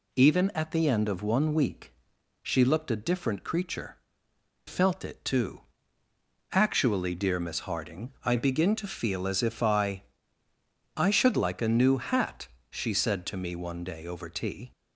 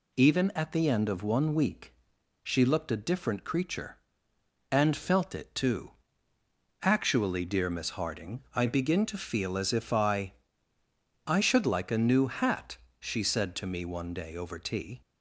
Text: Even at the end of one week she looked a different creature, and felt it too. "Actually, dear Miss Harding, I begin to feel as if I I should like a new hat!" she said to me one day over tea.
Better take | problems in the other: second | pauses between "week" and "she"; noticeable; at 1.9 s; 0.50 s long; noticeable in the second // skips "and"; at 4.3 s // pauses between "I" and "I"; noticeable; at 10.0 s; 0.92 s long; noticeable in the second

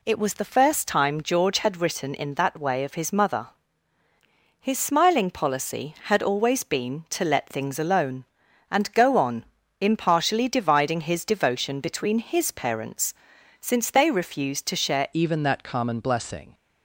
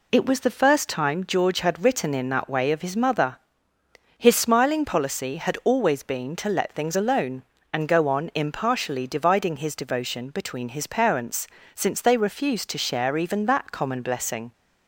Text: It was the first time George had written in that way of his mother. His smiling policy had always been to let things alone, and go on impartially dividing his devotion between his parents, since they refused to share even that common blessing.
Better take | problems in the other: second | pauses between "on" and "impartially"; slight; at 9.4 s; 0.36 s long // changes voice at "even"; from 15.1 s on; 1.4 s long

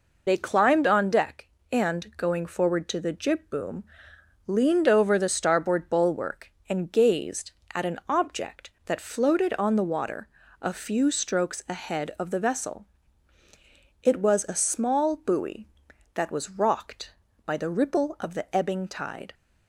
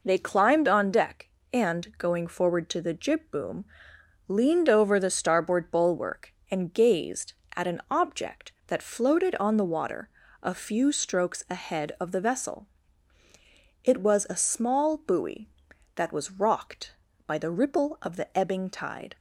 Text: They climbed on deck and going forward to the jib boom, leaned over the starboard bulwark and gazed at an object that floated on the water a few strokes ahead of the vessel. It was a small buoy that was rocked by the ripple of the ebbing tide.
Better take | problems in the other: second | loses the start of "They"; at 0.2 s; 40 ms // pauses between "water" and "a"; slight; at 10.2 s; 0.32 s long; slight in the second

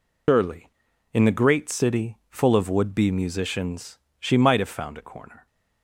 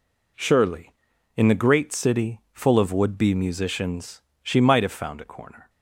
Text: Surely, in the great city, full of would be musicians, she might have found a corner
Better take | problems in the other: second | loses the start of "Surely"; at 0.2 s; 160 ms

